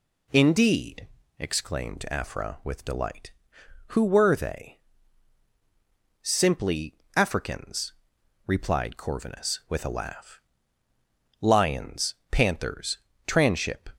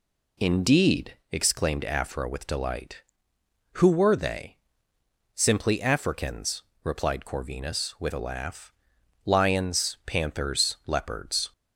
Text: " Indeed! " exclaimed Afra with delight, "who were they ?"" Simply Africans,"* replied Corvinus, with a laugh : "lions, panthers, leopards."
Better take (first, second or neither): second